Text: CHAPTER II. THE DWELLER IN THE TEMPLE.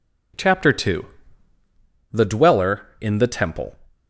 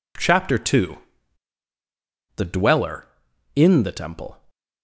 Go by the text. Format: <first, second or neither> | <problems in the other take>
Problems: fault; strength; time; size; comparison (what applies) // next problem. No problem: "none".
neither | none